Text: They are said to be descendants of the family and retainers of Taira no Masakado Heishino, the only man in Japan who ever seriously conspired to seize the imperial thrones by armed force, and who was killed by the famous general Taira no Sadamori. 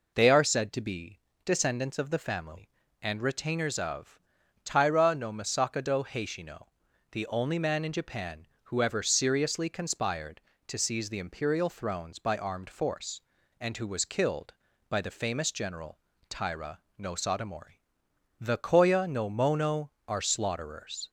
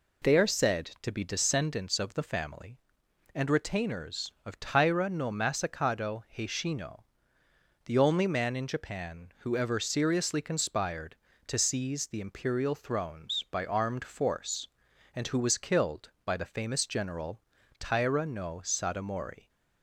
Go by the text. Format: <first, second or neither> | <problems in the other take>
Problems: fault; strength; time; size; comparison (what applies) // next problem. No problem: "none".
second | pauses between "be" and "descendants"; slight; at 1.2 s; 0.22 s long // pauses between "of" and "Taira"; at 4.1 s; 0.44 s long // pauses between "general" and "Taira"; slight; at 15.9 s; 0.30 s long; also in the second // pauses between "Taira" and "no"; slight; at 16.8 s; 0.18 s long // goes on to say "The koya no mono are slaughterers"; strong; from 18.3 s on; 2.7 s long